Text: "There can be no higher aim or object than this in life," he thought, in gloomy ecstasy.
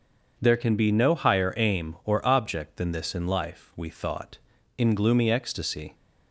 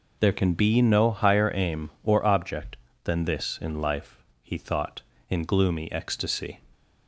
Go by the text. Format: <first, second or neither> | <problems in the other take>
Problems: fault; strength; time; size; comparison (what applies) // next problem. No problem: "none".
second | starts louder than the rest; until 1.3 s; 6.5 dB // says "we" for "he"; at 3.7 s